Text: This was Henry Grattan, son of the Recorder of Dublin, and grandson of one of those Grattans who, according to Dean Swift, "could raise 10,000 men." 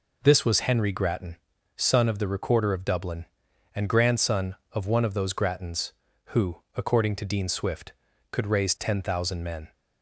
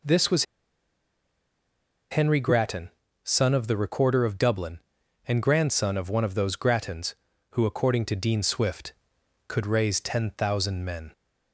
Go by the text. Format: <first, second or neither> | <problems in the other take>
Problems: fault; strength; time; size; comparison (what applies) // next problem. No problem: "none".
first | pauses between "was" and "Henry"; strong; at 0.4 s; 1.6 s long